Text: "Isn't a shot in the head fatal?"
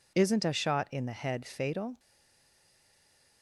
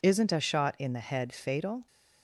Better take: second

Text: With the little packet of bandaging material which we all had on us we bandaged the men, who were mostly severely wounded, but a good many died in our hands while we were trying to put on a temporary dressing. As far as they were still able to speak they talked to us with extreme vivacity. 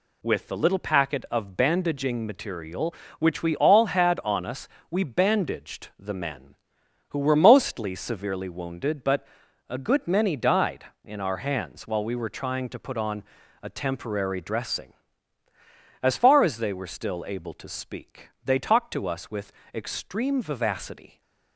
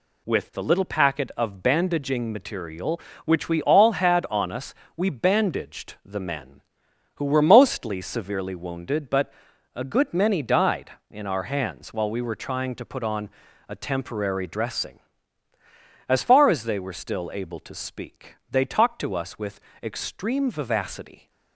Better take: neither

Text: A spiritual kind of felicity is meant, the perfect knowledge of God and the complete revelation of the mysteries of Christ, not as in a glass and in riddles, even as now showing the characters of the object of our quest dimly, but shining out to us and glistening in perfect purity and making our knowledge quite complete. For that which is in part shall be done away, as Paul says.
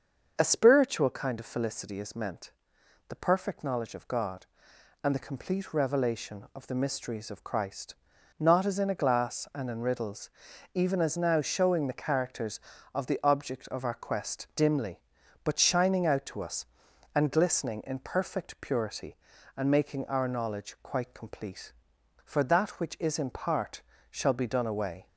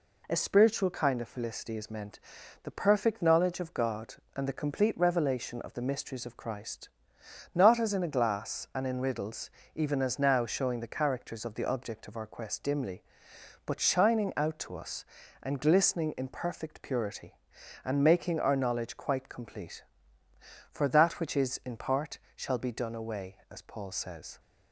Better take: second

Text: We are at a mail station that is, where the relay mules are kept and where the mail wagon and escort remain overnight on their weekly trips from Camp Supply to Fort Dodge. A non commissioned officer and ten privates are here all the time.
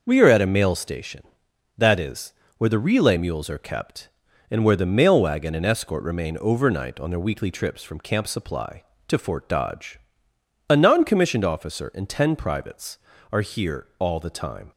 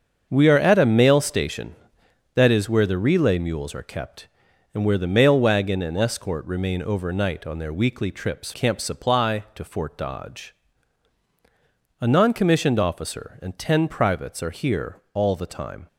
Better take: first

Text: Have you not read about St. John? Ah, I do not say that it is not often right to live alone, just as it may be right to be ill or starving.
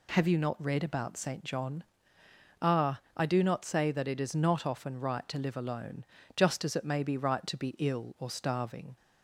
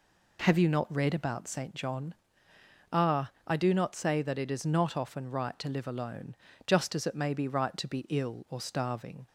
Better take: first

